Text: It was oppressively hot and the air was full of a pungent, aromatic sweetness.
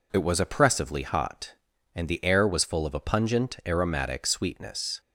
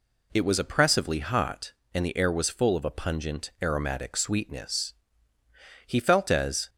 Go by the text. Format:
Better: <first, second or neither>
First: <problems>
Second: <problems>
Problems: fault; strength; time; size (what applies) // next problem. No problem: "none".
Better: first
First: none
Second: goes on to say "He felt as"; noticeable; from 5.8 s on; 0.82 s long